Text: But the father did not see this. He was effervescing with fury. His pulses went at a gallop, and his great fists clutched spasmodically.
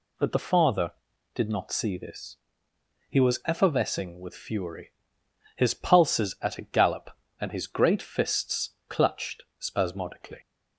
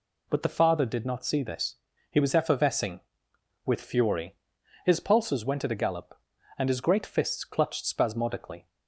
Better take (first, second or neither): second